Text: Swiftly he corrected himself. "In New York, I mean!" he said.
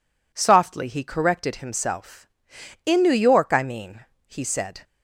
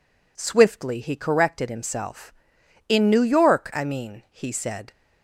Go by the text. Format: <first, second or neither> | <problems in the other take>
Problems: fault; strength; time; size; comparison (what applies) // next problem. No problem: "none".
second | says "Softly" for "Swiftly"; at 0.3 s